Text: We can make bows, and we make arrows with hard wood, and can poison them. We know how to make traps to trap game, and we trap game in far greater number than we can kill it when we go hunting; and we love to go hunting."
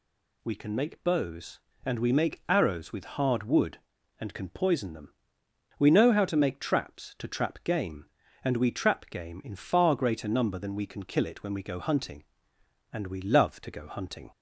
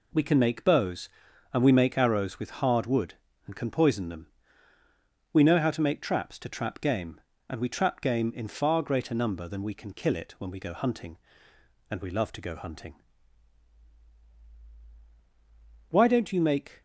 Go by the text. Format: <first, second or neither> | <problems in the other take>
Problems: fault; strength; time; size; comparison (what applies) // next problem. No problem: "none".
first | goes on to say "Why don't you make"; noticeable; from 15.9 s on; 0.88 s long